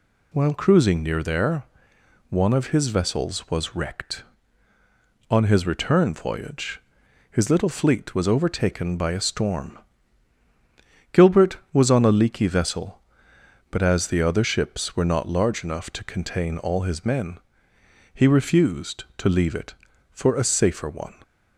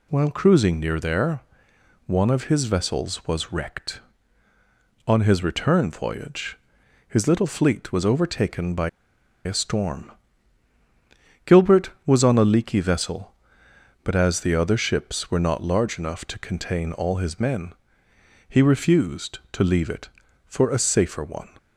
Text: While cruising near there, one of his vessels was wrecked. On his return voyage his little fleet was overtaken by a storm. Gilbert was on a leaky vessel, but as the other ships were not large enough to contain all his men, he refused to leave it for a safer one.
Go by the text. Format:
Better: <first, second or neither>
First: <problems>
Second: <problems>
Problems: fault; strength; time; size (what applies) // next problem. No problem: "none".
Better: first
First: pauses between "voyage" and "his"; noticeable; at 6.8 s; 0.49 s long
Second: pauses between "voyage" and "his"; noticeable; at 6.5 s; 0.50 s long // pauses between "by" and "a"; noticeable; at 8.8 s; 0.55 s long